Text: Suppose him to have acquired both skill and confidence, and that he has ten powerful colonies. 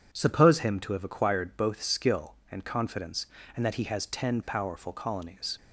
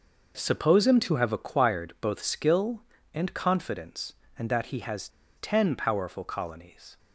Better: first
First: none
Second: pauses between "has" and "ten"; slight; at 5.0 s; 0.29 s long

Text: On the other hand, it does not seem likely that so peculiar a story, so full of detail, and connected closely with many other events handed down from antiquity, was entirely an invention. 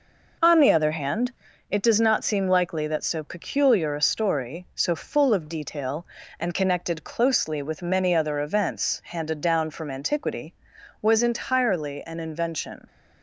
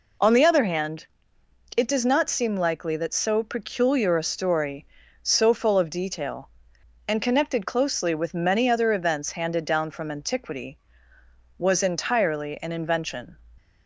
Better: neither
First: none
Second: none

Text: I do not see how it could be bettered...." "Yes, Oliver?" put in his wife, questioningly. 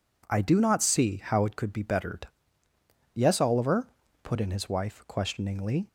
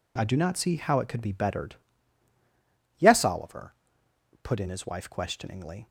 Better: neither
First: none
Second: none

